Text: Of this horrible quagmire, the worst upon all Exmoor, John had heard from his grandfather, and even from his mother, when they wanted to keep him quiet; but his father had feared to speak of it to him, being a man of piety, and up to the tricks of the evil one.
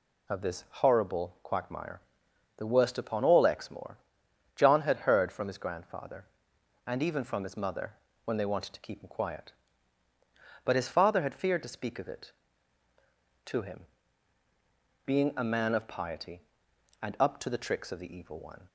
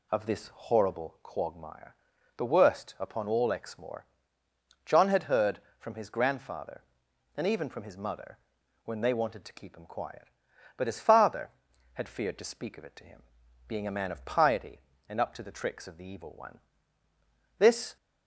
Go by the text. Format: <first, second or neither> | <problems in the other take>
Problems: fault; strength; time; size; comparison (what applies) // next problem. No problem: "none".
first | goes on to say "This"; slight; from 17.5 s on; 0.38 s long